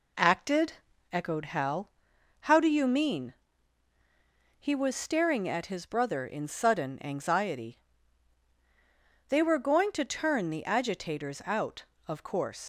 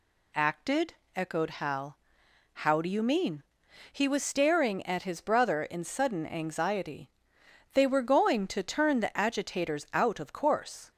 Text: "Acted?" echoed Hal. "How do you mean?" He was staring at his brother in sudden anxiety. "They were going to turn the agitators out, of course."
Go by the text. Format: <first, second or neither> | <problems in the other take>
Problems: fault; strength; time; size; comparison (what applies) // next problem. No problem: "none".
second | leaves "course" unfinished; at 12.6 s; 85 ms